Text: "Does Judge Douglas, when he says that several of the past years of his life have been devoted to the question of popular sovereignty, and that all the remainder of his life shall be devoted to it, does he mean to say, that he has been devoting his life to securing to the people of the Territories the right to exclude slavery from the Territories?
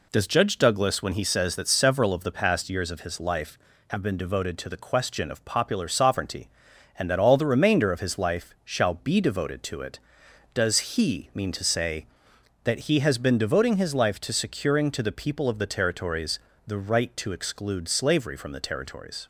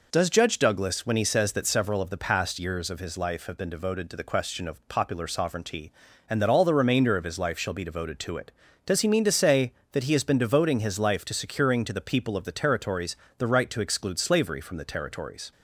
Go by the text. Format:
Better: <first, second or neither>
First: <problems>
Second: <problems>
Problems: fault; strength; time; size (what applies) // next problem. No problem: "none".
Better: neither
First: pauses between "Territories" and "the"; slight; at 16.3 s; 0.26 s long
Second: pauses between "Territories" and "the"; slight; at 13.1 s; 0.24 s long